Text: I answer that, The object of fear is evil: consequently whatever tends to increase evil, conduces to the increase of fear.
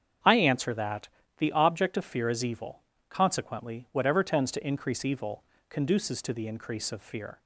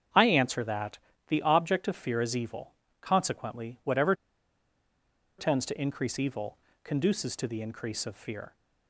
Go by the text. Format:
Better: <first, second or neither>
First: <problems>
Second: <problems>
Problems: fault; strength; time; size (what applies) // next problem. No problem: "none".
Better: first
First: starts louder than the rest; strong; until 1.5 s; 8 dB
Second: starts louder than the rest; strong; until 1.4 s; 8 dB // pauses between "whatever" and "tends"; strong; at 4.1 s; 1.2 s long